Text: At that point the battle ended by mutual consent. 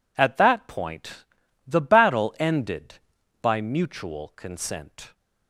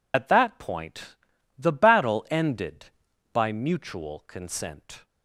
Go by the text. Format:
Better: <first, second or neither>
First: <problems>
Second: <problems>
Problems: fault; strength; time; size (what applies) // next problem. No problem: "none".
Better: first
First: pauses between "point" and "the"; at 1.2 s; 0.42 s long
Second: loses the start of "At"; at 0.1 s; 60 ms // pauses between "point" and "the"; at 1.1 s; 0.42 s long